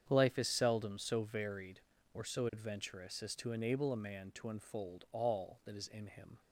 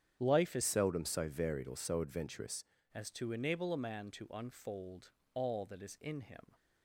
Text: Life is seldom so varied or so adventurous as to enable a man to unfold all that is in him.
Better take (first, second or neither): first